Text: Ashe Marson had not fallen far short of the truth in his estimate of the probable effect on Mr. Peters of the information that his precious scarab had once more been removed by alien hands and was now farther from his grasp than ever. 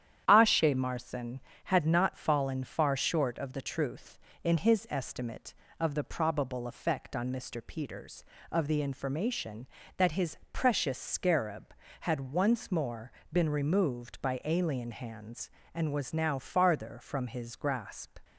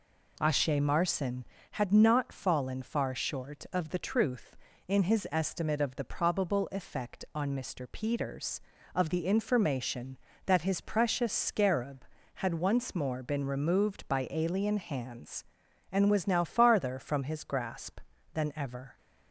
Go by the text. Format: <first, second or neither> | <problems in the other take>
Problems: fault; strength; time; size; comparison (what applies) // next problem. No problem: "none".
second | starts louder than the rest; strong; until 1.2 s; 10 dB // pauses between "his" and "precious"; slight; at 10.3 s; 0.16 s long // pauses between "more" and "been"; slight; at 13.1 s; 0.22 s long // stops before "than ever"; at 18.2 s